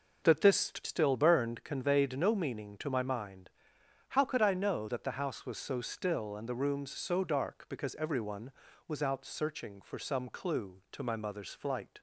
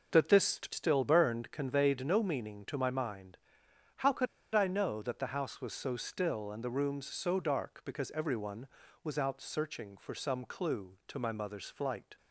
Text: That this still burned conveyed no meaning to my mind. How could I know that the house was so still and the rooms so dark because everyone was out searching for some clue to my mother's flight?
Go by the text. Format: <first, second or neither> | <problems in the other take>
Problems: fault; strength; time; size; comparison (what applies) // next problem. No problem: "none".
first | starts louder than the rest; until 1.2 s; 7 dB; also in the first // pauses between "could" and "I"; slight; at 4.2 s; 0.27 s long